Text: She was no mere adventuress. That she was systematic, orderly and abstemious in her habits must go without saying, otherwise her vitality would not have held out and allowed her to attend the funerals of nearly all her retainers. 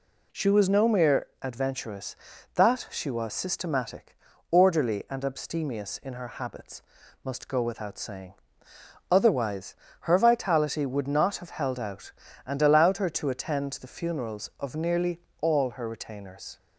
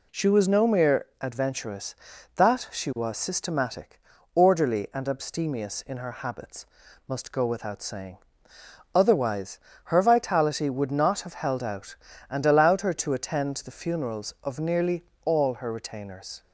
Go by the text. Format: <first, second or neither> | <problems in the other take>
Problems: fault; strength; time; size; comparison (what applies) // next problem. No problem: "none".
neither | pauses between "mere" and "adventuress"; slight; the same in both // pauses between "habits" and "must"; the same in both // pauses between "otherwise" and "her"; slight; the same in both // pauses between "nearly" and "all"; slight; the same in both